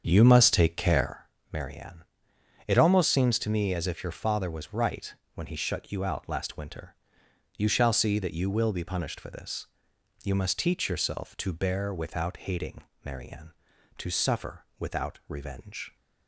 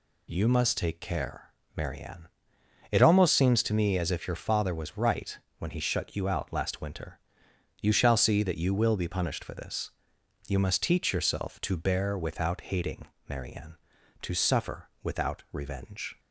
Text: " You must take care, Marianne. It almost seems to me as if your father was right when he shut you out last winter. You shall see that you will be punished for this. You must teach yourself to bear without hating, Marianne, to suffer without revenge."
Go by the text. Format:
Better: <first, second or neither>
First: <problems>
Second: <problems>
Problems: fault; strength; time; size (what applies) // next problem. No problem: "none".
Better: second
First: starts louder than the rest; strong; until 1.3 s; 7 dB // pauses between "right" and "when"; slight; at 5.1 s; 0.22 s long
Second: pauses between "right" and "when"; slight; at 5.3 s; 0.22 s long